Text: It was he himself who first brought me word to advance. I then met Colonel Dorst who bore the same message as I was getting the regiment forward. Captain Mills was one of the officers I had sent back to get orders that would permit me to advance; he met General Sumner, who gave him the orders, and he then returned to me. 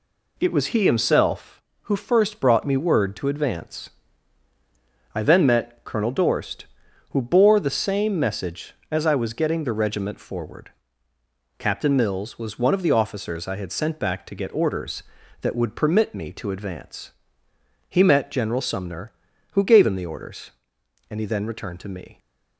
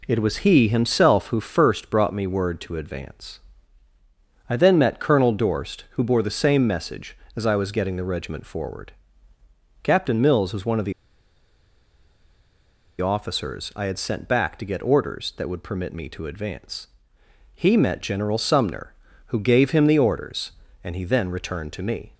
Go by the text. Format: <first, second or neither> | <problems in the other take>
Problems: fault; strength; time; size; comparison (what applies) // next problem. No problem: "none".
first | pauses between "the" and "officers"; strong; at 10.9 s; 2.0 s long